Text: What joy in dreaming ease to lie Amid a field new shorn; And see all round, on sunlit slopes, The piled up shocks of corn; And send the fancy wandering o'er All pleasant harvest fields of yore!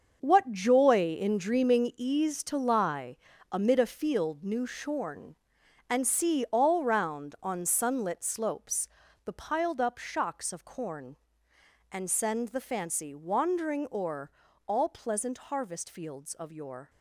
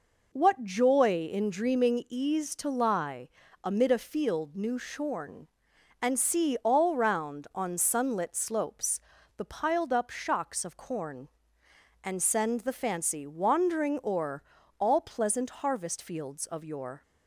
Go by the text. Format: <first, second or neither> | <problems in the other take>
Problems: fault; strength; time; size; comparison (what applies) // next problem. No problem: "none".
second | gets quieter; strong; throughout; 10.5 dB // pauses between "lie" and "Amid"; slight; at 3.1 s; 0.36 s long; slight in the second // pauses between "o'er" and "All"; at 14.2 s; 0.38 s long; also in the second